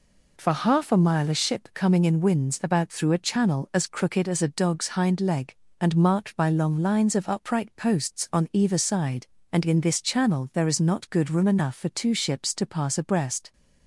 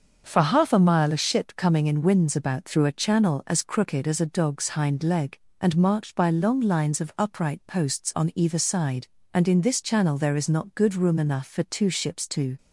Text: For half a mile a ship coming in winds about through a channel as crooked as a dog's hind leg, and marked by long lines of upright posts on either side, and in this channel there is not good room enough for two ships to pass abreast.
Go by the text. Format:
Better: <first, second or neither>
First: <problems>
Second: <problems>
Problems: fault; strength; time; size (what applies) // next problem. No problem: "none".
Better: first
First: none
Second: starts louder than the rest; until 1.2 s; 6.5 dB // stops before "pass abreast"; at 12.5 s